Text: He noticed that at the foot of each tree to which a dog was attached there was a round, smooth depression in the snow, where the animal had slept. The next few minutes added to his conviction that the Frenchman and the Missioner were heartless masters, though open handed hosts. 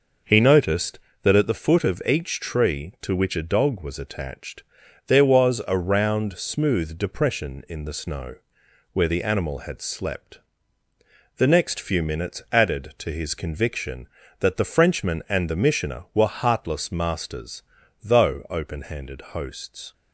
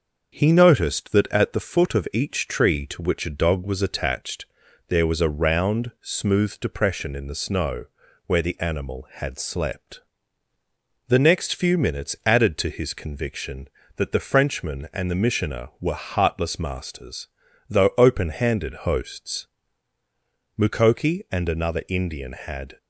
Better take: first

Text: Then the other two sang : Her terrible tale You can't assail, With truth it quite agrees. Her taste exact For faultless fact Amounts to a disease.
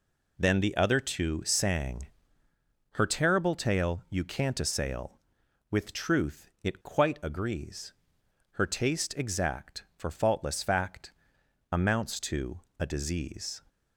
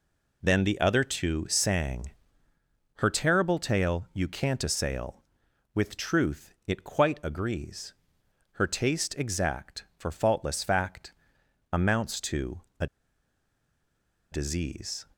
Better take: first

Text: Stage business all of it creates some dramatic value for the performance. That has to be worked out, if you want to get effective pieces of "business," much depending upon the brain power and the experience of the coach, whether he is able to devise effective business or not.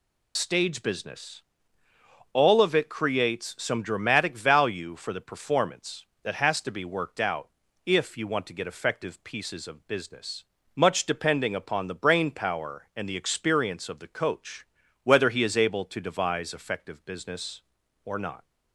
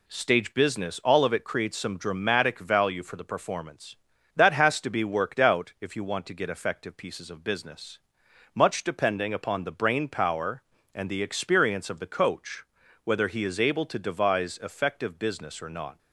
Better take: second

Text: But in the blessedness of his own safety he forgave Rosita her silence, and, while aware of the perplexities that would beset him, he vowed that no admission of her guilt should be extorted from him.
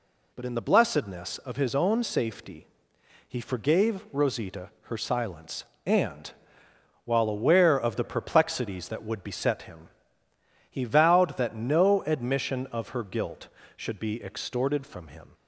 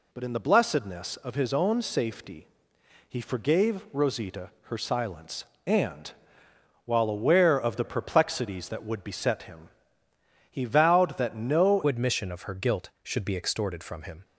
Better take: first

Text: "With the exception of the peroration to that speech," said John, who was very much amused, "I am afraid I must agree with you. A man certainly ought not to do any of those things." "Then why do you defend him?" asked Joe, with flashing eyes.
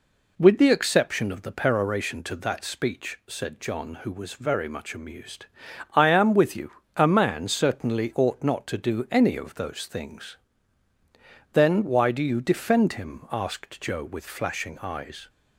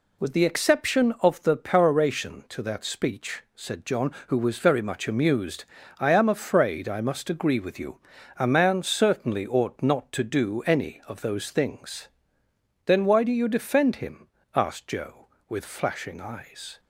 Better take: second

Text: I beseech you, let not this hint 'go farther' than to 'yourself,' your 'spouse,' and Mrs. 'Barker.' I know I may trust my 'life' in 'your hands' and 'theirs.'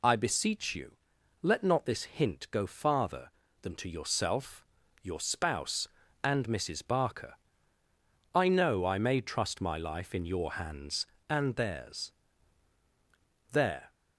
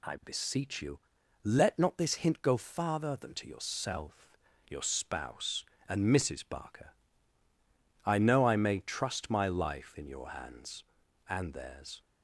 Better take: second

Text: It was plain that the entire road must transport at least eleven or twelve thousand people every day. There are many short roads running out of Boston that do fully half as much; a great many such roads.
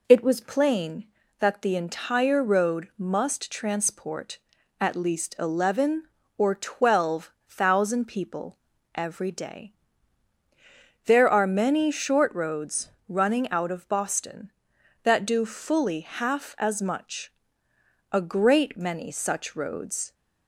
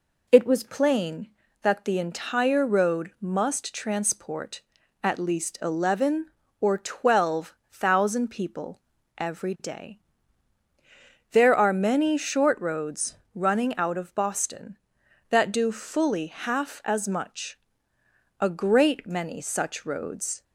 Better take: neither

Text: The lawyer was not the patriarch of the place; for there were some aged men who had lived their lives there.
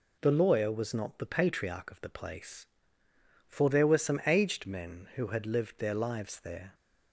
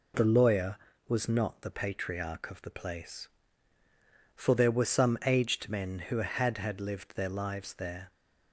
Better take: first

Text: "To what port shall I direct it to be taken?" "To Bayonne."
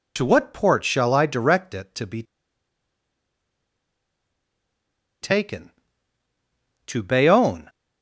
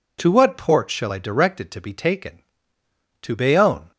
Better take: second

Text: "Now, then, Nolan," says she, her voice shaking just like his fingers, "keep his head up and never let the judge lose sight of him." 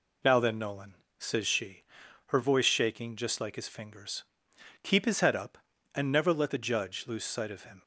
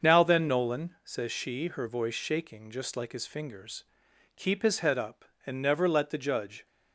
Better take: first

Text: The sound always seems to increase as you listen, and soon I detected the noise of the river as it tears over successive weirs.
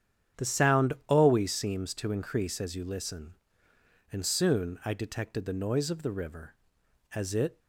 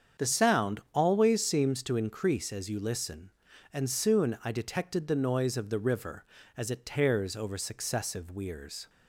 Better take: second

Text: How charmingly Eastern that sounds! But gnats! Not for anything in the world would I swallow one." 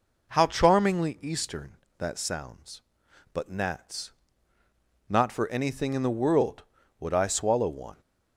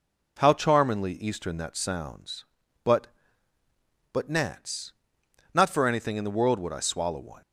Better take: first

